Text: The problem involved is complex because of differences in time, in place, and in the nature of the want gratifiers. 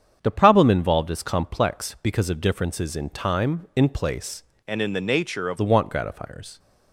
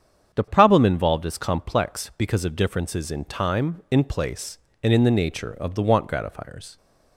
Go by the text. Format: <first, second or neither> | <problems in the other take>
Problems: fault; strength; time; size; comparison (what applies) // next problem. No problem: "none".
second | starts louder than the rest; strong; until 1.2 s; 8 dB; strong in the second // changes voice from "and" to "of"; from 4.6 to 5.5 s; 0.9 s long